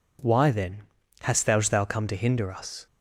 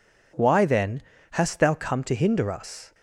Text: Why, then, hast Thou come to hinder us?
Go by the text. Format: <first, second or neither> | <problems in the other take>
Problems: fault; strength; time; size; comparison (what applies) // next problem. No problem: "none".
second | says "Thou" twice; at 1.5 s